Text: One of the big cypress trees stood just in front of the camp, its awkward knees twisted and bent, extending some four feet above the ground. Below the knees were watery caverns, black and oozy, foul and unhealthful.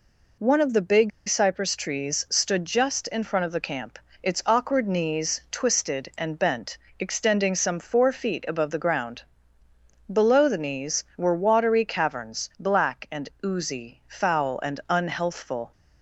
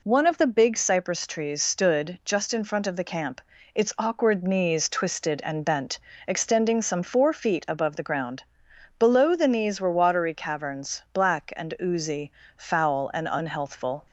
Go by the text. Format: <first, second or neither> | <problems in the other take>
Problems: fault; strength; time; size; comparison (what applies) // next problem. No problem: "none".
second | pauses between "big" and "cypress"; slight; at 1.1 s; 0.19 s long